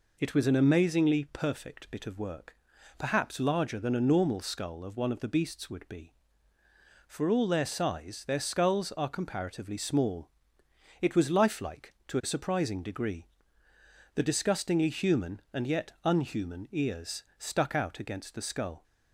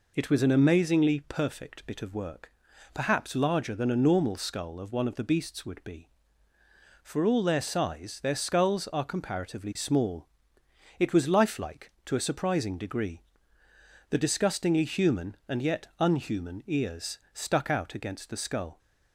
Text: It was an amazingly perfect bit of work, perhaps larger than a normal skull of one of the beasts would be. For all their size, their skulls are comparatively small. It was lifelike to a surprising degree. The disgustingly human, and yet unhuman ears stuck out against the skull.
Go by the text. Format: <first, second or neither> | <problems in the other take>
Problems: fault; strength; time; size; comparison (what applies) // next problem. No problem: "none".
neither | pauses between "ears" and "stuck"; slight; the same in both